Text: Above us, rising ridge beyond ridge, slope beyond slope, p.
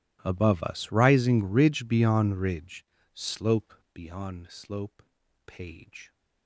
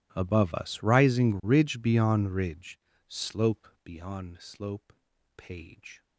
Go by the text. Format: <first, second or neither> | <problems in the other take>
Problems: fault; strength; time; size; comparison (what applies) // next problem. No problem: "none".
neither | pauses between "slope" and "beyond"; slight; the same in both